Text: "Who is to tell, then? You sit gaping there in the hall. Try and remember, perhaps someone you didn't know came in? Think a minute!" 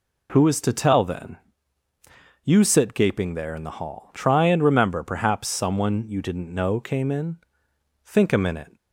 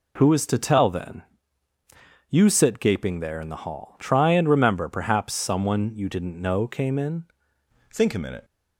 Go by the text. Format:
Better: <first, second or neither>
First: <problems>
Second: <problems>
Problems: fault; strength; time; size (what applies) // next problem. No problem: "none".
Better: first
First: none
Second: changes voice at "Think"; from 7.9 s on; 0.5 s long